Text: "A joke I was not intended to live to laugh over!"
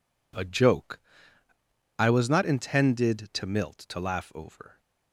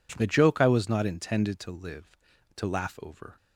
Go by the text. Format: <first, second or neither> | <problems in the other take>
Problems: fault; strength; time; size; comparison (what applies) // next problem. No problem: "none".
second | pauses between "joke" and "I"; noticeable; at 1.0 s; 0.96 s long // says "milt" for "live"; at 3.4 s